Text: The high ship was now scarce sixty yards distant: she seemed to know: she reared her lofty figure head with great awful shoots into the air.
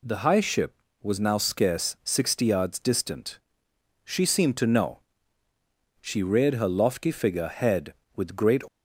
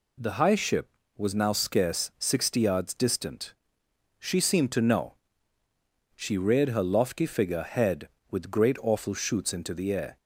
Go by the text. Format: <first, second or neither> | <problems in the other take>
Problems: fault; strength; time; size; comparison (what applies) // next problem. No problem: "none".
second | stops before "awful shoots into the air"; at 8.6 s